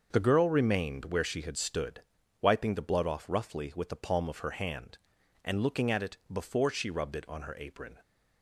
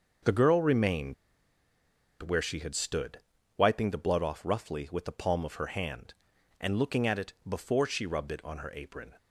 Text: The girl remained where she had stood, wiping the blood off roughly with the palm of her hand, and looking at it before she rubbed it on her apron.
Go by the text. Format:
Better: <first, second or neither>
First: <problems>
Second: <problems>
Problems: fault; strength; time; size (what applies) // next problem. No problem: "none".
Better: first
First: starts louder than the rest; noticeable; until 1.1 s; 6 dB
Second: starts louder than the rest; noticeable; until 2.3 s; 6 dB // pauses between "remained" and "where"; at 1.1 s; 1.0 s long